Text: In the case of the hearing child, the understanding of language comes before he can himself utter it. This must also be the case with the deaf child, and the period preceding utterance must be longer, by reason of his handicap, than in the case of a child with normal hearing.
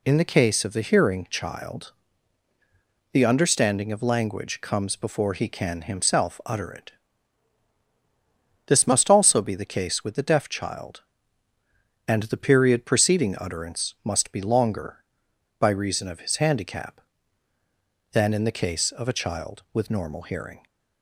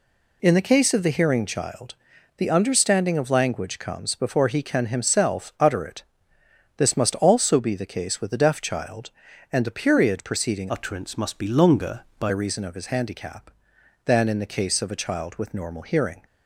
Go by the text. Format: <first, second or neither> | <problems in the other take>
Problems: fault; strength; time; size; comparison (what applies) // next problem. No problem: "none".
first | changes voice from "utterance" to "by"; from 10.6 to 12.2 s; 1.6 s long